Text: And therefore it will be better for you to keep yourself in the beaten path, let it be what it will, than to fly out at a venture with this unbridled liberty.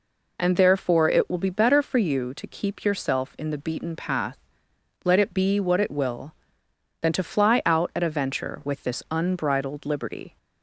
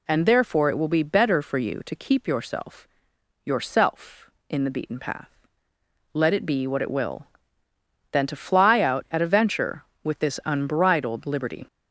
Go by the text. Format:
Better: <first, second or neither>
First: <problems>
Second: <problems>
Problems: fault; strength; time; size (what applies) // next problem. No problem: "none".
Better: first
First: none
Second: says "yourself" twice; at 3.4 s